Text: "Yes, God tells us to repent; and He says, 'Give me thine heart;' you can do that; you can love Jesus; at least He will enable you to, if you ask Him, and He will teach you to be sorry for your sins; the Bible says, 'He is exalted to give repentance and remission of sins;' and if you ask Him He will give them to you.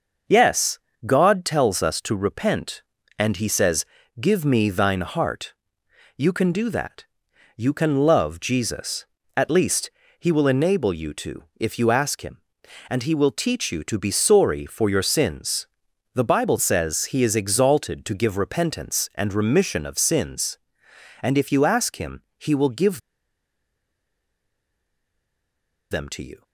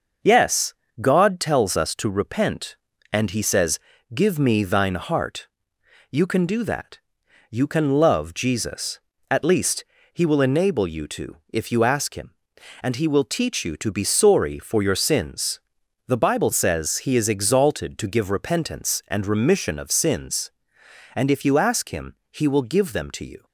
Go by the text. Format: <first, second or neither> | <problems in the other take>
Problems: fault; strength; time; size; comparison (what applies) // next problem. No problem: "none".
second | starts louder than the rest; until 1.5 s; 6 dB; also in the second // pauses between "least" and "He"; slight; at 9.9 s; 0.26 s long; slight in the second // pauses between "give" and "them"; strong; at 22.9 s; 2.9 s long